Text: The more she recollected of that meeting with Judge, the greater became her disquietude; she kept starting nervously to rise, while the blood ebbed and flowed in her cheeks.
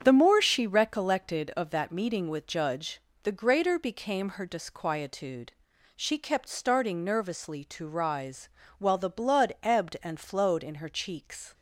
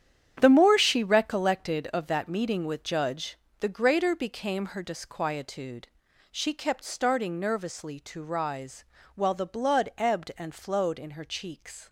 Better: first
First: starts louder than the rest; strong; until 1.0 s; 7.5 dB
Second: gets quieter; strong; throughout; 10.5 dB // starts louder than the rest; strong; until 1.4 s; 9.5 dB

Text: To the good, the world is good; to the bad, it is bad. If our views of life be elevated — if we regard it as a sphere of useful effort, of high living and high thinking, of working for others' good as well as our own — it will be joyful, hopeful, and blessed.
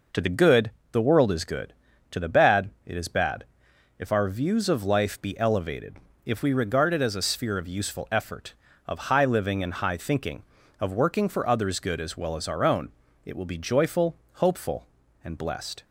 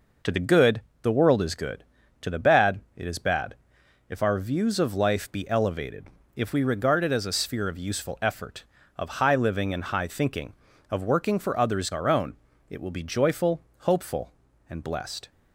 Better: first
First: none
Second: skips "good as well as"; at 11.9 s

